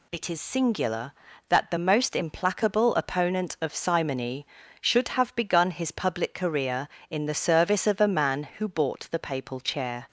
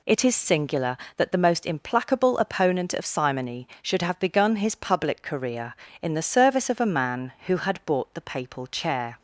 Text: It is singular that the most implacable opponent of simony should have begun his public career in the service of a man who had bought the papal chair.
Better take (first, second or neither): second